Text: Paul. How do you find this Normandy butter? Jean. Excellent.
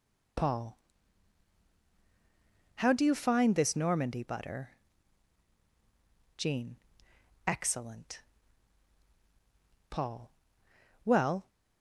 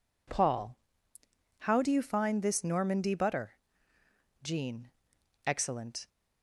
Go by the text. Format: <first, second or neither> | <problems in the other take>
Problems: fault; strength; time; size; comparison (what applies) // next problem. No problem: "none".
second | goes on to say "Paul Well"; from 9.9 s on; 1.5 s long